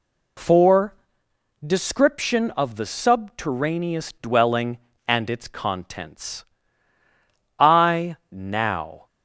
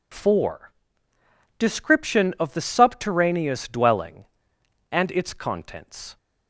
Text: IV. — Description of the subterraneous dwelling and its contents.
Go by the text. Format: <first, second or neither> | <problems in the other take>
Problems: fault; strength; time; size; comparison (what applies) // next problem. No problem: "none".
second | goes on to say "I now"; from 7.5 s on; 1.4 s long